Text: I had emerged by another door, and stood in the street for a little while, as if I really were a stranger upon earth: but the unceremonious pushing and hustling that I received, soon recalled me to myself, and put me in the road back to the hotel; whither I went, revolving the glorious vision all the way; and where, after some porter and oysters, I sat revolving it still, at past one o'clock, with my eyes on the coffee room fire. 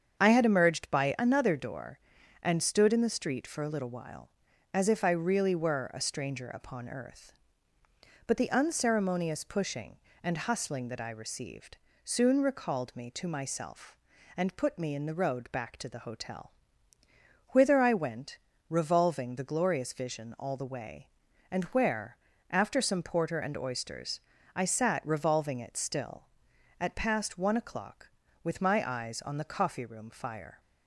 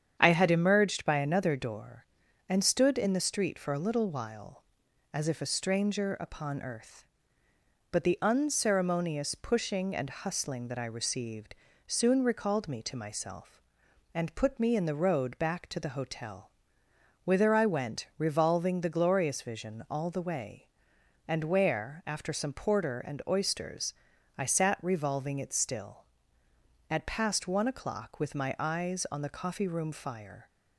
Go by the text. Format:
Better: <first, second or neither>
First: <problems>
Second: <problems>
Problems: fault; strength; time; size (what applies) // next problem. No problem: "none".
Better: first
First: starts louder than the rest; strong; until 1.2 s; 7.5 dB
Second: starts louder than the rest; strong; until 1.2 s; 8.5 dB // skips "I really were"; at 5.4 s